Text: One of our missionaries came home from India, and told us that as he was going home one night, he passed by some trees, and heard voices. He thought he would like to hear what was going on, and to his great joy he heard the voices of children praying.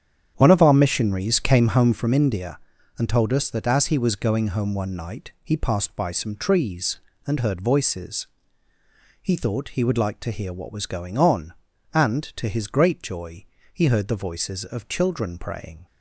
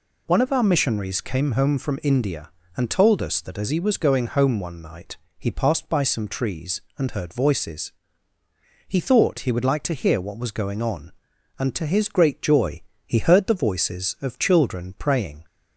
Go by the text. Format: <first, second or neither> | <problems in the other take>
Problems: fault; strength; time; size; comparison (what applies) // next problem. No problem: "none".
second | starts louder than the rest; strong; until 2.1 s; 9 dB // pauses between "joy" and "he"; slight; at 13.4 s; 0.28 s long; slight in the second